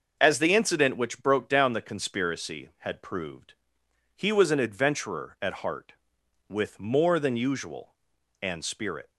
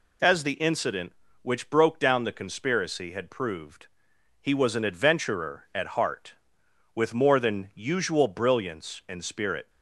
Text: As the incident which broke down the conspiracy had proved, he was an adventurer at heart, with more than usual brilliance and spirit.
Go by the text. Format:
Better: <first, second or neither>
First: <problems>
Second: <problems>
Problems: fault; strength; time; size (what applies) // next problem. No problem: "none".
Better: second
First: starts louder than the rest; until 1.2 s; 6 dB // skips "brilliance"; at 8.1 s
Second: none